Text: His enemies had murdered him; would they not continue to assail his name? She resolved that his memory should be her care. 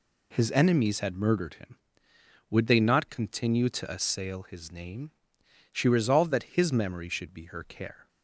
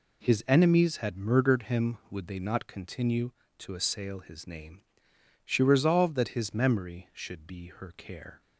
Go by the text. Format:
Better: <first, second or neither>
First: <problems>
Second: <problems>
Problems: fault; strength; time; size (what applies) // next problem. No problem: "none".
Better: neither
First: none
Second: none